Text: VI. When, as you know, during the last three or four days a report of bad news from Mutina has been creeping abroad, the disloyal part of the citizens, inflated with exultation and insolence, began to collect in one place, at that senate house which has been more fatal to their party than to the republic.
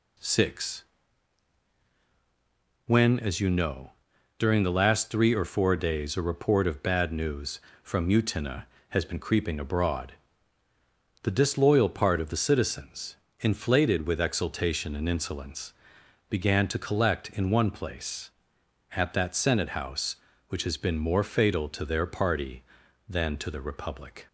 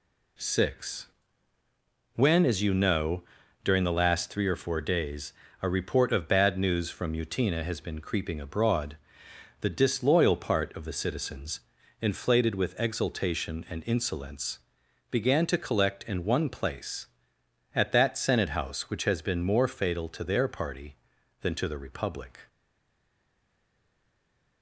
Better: first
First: none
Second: pauses between "days" and "a"; slight; at 5.3 s; 0.30 s long // stays silent after the last word; from 22.4 s on; 2.2 s long

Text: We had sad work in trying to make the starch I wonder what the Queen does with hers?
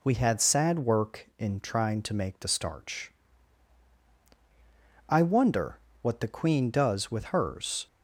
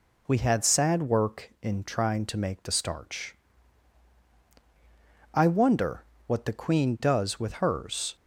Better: neither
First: pauses between "starch" and "I"; strong; at 3.1 s; 1.9 s long // pauses between "wonder" and "what"; slight; at 5.7 s; 0.24 s long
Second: pauses between "starch" and "I"; strong; at 3.3 s; 1.9 s long // pauses between "wonder" and "what"; slight; at 6.0 s; 0.24 s long

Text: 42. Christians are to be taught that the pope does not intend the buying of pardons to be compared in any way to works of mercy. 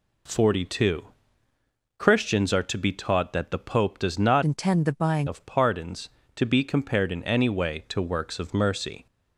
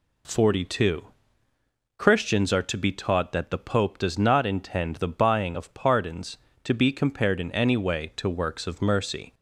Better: second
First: changes voice from "intend" to "buying"; from 4.4 to 5.2 s; 0.8 s long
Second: none

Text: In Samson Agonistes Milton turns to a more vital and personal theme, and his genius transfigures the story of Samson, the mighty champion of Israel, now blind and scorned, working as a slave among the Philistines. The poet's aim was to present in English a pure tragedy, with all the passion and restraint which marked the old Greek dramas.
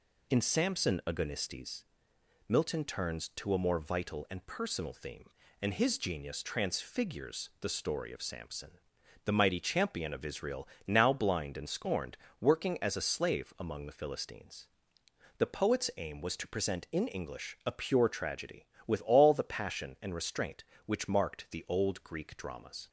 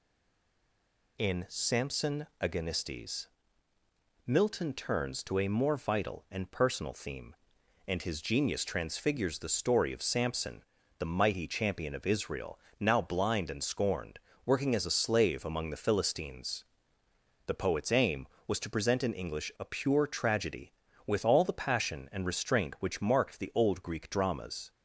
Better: first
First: pauses between "Agonistes" and "Milton"; noticeable; at 1.8 s; 0.66 s long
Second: stays silent before the first word; noticeable; until 1.1 s; 1.1 s long // pauses between "Agonistes" and "Milton"; noticeable; at 3.2 s; 0.98 s long

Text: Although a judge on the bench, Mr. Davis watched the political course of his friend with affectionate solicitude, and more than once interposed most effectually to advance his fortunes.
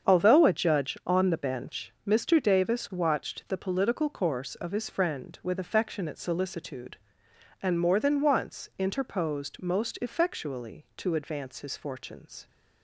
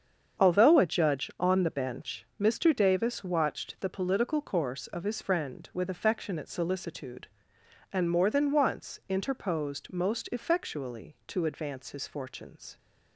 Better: neither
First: starts louder than the rest; strong; until 1.1 s; 7.5 dB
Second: starts louder than the rest; strong; until 1.4 s; 7.5 dB

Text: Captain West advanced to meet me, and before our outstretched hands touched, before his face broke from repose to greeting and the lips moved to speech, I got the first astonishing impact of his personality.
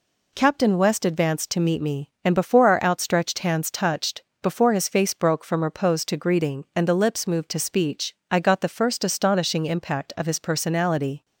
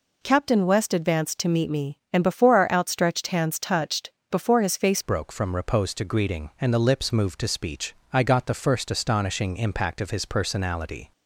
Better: first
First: none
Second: changes voice at "broke"; from 5.0 s on; 6.1 s long

